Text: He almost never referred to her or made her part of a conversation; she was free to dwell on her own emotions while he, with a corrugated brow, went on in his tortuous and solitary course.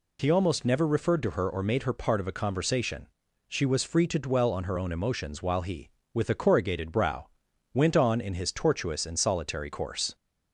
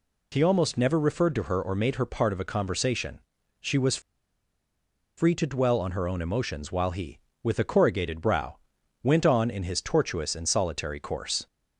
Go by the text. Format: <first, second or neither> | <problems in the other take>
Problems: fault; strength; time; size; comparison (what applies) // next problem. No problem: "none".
first | pauses between "was" and "free"; at 4.0 s; 1.1 s long